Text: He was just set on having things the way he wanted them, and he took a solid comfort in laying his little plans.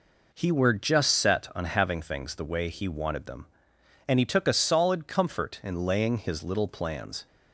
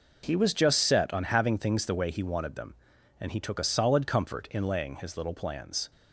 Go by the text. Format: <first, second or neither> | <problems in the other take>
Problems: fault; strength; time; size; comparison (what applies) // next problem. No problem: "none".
second | says "were" for "was"; at 0.5 s